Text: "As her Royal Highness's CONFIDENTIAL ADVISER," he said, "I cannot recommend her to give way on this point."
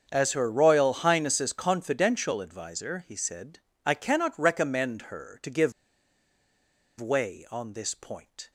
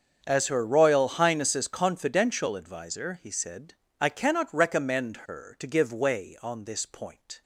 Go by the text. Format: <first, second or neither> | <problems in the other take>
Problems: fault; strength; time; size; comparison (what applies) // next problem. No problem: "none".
second | starts louder than the rest; until 1.1 s; 7 dB; strong in the second // pauses between "give" and "way"; strong; at 5.7 s; 1.2 s long